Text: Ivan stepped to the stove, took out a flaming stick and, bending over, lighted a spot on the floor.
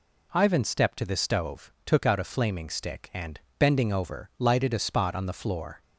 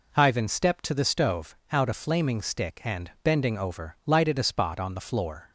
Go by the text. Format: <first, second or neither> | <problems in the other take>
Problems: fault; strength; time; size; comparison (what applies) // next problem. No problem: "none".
first | skips "took"; at 1.6 s